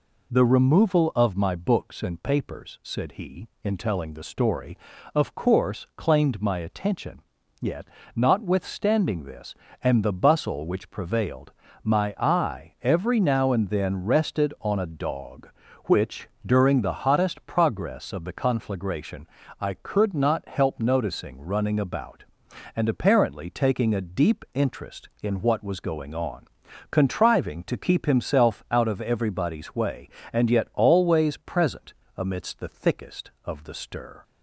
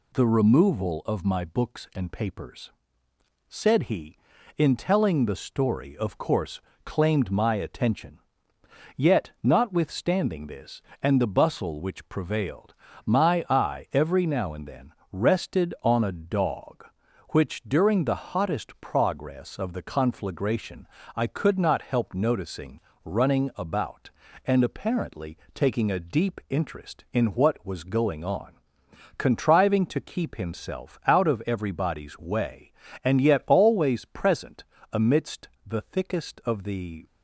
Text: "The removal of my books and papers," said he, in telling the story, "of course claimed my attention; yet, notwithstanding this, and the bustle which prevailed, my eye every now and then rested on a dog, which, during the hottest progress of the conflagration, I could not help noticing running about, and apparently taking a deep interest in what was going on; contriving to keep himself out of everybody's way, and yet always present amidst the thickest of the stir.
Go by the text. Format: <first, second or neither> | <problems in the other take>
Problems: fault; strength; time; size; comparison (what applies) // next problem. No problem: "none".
first | pauses between "course" and "claimed"; slight; at 6.6 s; 0.24 s long // pauses between "then" and "rested"; slight; at 14.9 s; 0.20 s long // pauses between "noticing" and "running"; slight; at 22.8 s; 0.22 s long // pauses between "apparently" and "taking"; slight; at 25.3 s; 0.16 s long // pauses between "present" and "amidst"; slight; at 34.6 s; 0.28 s long; slight in the first // pauses between "amidst" and "the"; slight; at 35.4 s; 0.18 s long // stops before "stir"; at 37.0 s